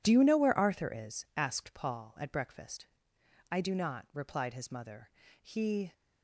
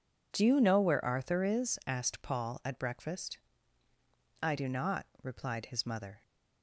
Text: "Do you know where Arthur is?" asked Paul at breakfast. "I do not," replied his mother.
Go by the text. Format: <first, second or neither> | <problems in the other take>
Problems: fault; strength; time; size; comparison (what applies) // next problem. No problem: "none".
second | goes on to say "He"; from 5.4 s on; 0.52 s long